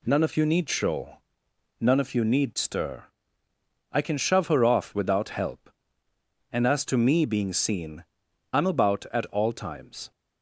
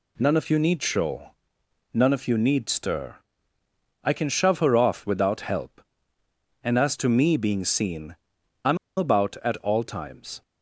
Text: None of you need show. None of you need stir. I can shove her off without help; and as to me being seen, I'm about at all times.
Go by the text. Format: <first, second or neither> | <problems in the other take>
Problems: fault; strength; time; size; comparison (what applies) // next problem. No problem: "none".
first | pauses between "I'm" and "about"; slight; at 8.7 s; 0.20 s long